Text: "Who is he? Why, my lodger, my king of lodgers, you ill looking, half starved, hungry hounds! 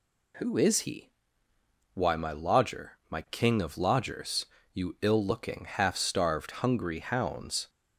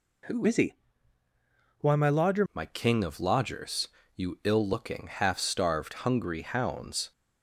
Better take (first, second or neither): first